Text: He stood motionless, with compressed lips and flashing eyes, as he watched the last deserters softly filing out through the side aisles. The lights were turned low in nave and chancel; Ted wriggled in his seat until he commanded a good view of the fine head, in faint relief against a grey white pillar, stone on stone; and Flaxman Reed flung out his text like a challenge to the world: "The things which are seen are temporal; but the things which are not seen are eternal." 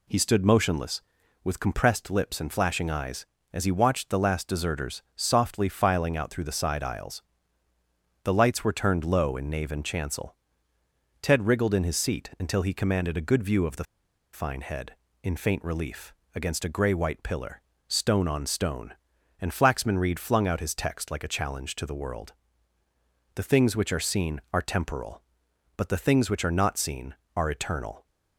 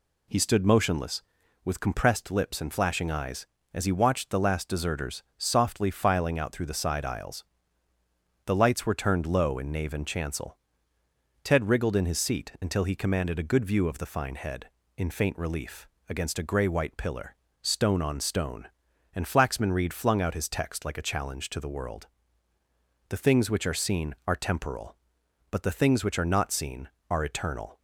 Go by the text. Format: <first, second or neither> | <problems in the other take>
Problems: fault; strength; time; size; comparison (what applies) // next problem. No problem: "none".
second | pauses between "the" and "fine"; noticeable; at 13.8 s; 0.48 s long // pauses between "relief" and "against"; slight; at 16.1 s; 0.20 s long; slight in the second